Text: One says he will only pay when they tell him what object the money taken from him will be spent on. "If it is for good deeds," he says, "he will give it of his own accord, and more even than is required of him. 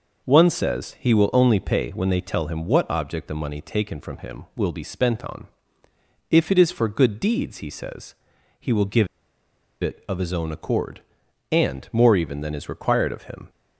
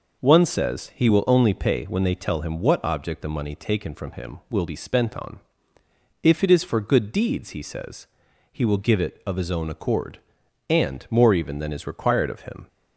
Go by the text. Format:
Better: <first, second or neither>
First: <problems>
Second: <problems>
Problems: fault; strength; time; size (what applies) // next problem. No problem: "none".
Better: second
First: pauses between "give" and "it"; noticeable; at 9.0 s; 0.76 s long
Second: none